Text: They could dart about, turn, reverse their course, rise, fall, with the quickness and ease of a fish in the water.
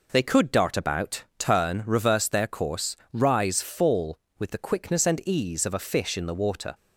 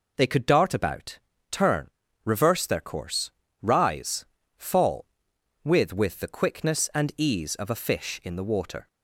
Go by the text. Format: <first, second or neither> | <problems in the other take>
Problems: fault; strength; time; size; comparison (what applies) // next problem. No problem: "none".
first | says "with" twice; at 5.9 s